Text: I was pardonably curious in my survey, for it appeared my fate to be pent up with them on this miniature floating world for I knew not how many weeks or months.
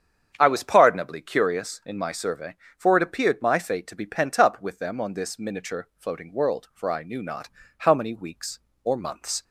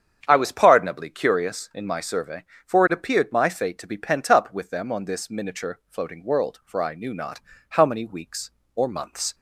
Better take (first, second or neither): neither